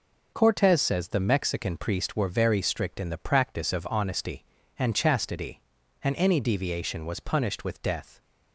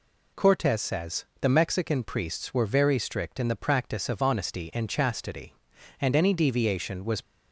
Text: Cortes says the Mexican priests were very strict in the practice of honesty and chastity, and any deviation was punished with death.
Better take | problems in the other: first | pauses between "says" and "the"; slight; at 1.2 s; 0.16 s long // stops before "punished with death"; at 7.2 s

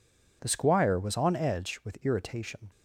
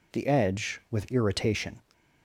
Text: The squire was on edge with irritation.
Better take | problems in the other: first | skips "squire was on"; at 0.2 s

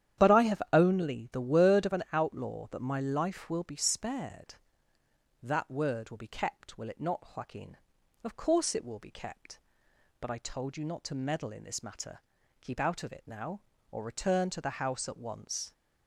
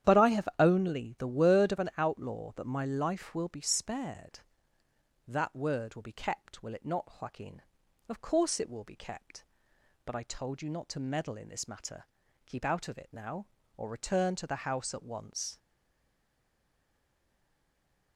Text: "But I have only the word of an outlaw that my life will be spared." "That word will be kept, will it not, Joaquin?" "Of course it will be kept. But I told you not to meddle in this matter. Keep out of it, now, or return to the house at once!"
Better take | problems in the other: first | starts louder than the rest; strong; until 1.2 s; 10 dB; strong in the first // stays silent after the last word; strong; from 15.5 s on; 2.6 s long

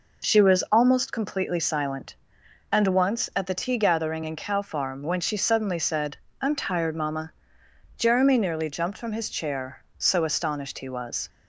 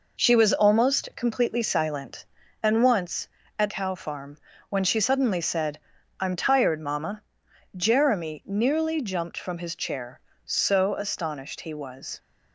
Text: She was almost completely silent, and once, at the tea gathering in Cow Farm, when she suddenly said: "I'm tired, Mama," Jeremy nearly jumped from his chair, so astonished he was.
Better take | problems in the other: first | skips "the tea gathering in"; at 3.6 s

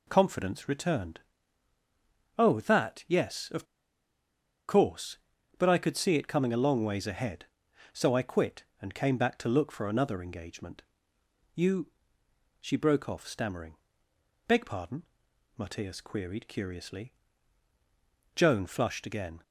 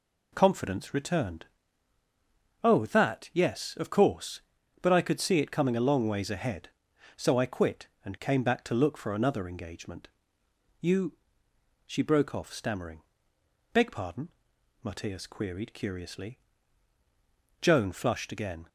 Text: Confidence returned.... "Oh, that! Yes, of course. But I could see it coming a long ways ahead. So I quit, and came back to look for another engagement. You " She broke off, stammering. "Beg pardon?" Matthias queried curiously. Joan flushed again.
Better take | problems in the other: second | pauses between "of" and "course"; at 3.6 s; 1.0 s long

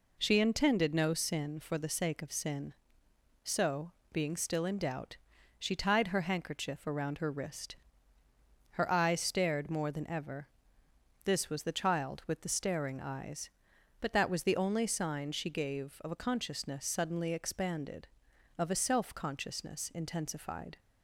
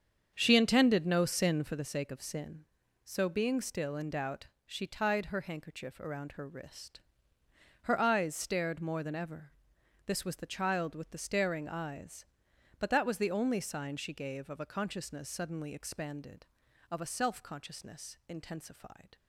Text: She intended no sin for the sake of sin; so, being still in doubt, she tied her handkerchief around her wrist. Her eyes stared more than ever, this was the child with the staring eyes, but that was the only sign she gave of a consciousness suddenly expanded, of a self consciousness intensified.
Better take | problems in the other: first | starts louder than the rest; strong; until 1.8 s; 7.5 dB

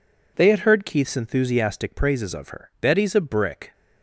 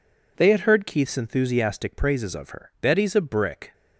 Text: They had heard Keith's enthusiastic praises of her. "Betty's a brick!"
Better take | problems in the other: neither | none

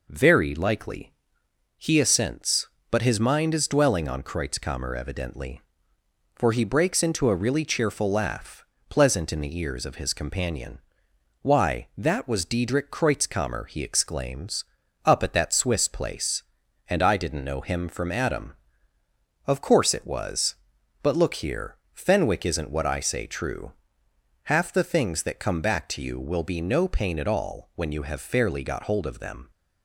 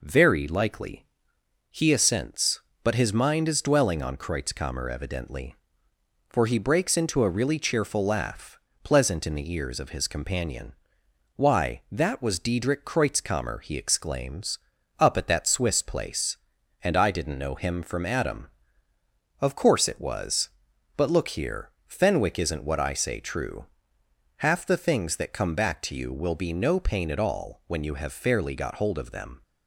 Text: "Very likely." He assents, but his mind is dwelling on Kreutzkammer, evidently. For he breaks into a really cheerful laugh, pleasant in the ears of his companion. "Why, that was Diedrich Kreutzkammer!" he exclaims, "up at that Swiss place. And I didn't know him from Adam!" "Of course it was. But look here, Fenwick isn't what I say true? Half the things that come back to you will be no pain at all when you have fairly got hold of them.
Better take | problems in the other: neither | none

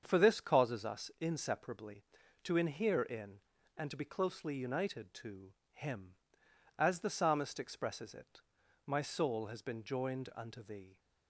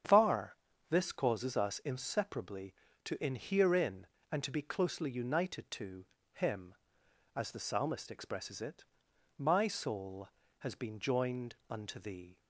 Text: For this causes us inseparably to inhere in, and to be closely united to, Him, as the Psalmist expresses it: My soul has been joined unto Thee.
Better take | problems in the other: first | starts louder than the rest; strong; until 1.4 s; 8.5 dB; strong in the first // says "Far" for "For"; at 0.0 s // pauses between "joined" and "unto"; slight; at 11.5 s; 0.16 s long

